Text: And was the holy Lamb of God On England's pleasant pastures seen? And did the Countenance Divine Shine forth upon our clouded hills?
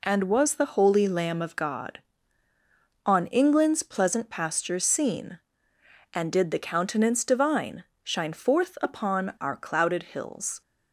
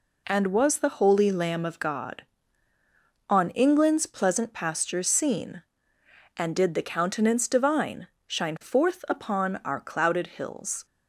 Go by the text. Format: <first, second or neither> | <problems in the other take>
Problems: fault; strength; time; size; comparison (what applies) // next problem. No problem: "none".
neither | pauses between "Divine" and "Shine"; slight; the same in both